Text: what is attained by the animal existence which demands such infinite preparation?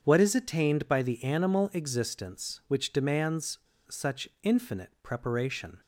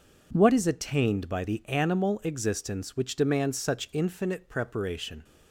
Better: second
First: starts louder than the rest; until 1.0 s; 7 dB // pauses between "demands" and "such"; slight; at 3.5 s; 0.29 s long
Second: none

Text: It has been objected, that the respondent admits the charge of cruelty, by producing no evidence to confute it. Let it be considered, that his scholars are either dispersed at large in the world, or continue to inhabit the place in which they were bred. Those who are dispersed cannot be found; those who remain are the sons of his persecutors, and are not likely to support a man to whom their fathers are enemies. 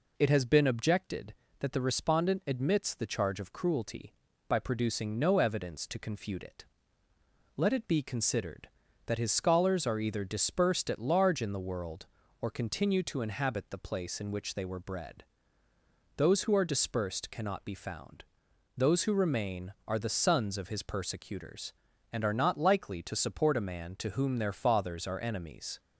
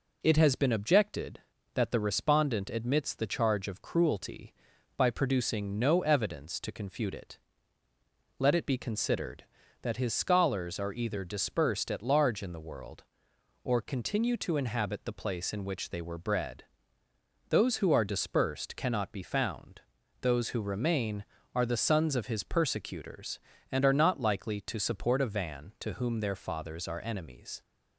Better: first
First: none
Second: says "van" for "man"; at 25.2 s

